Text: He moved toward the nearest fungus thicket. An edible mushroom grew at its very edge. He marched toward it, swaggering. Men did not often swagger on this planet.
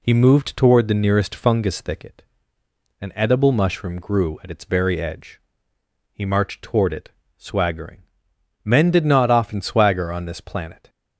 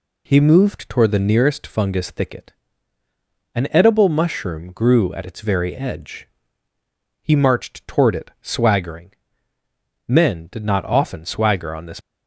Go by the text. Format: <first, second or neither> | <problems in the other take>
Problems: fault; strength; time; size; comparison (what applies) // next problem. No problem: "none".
first | stops before "planet"; at 12.0 s